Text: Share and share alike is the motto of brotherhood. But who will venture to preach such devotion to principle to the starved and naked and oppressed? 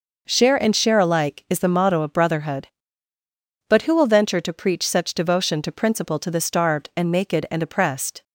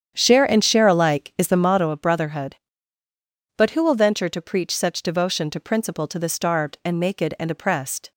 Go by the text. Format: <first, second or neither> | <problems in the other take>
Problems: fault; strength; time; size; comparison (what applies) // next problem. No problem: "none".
first | starts louder than the rest; strong; until 1.9 s; 8.5 dB